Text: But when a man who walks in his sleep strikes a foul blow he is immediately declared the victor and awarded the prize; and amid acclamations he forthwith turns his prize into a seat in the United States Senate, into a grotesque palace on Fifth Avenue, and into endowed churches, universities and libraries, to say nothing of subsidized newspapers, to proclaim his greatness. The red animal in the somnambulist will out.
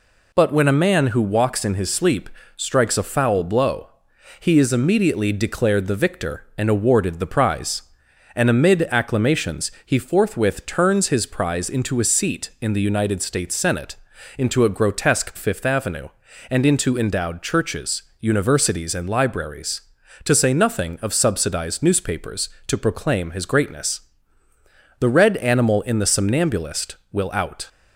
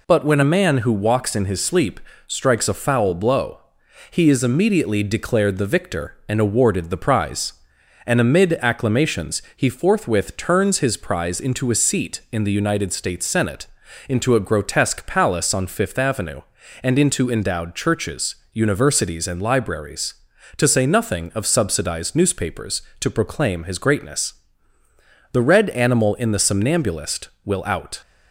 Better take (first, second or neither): second